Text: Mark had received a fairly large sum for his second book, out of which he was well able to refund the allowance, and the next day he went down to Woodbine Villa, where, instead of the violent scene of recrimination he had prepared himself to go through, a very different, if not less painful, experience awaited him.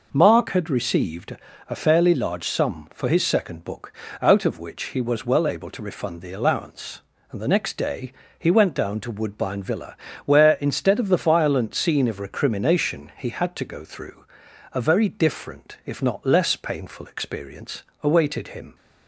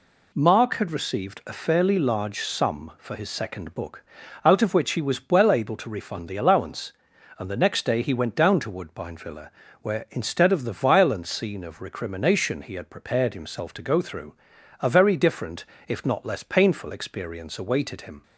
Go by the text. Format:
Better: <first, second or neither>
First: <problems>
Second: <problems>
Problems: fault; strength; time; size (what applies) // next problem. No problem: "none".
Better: second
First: pauses between "received" and "a"; slight; at 1.3 s; 0.32 s long // pauses between "day" and "he"; slight; at 8.1 s; 0.26 s long // skips "prepared himself"; at 13.5 s // pauses between "experience" and "awaited"; slight; at 17.8 s; 0.20 s long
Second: none